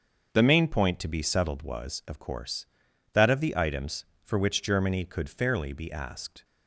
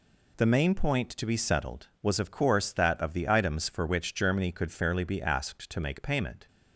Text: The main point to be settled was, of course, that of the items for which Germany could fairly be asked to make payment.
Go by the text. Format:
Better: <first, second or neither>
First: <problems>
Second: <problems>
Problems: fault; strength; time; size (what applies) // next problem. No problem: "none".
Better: second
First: starts louder than the rest; until 1.3 s; 6.5 dB // stops before "to make payment"; at 6.4 s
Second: none